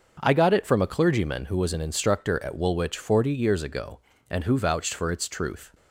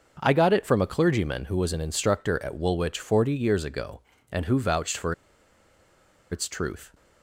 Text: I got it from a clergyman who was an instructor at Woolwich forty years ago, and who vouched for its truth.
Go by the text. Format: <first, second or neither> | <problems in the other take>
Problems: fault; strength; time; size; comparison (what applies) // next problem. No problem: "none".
first | starts louder than the rest; until 1.2 s; 6.5 dB; also in the first // pauses between "for" and "its"; at 5.1 s; 1.1 s long